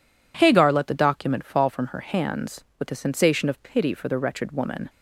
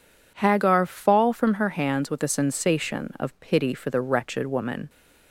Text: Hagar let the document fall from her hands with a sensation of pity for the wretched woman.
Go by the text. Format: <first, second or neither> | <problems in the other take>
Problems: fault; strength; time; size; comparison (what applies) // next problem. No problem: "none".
first | skips "let the document"; at 0.8 s